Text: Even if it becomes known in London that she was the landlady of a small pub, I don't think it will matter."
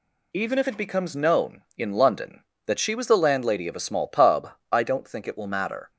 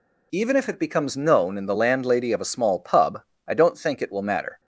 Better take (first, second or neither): first